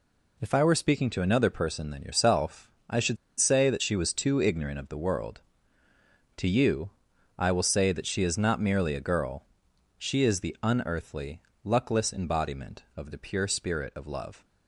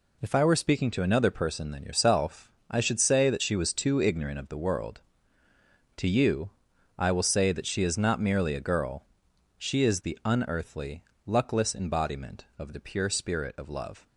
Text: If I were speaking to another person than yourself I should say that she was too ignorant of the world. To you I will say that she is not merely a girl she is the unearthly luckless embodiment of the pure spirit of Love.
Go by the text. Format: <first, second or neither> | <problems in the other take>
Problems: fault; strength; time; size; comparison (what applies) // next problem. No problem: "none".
second | pauses between "yourself" and "I"; slight; at 2.6 s; 0.20 s long; slight in the second // pauses between "should" and "say"; slight; at 3.1 s; 0.23 s long // pauses between "you" and "I"; noticeable; at 6.9 s; 0.48 s long; noticeable in the second // pauses between "girl" and "she"; noticeable; at 9.4 s; 0.52 s long; noticeable in the second // pauses between "unearthly" and "luckless"; slight; at 11.4 s; 0.22 s long; slight in the second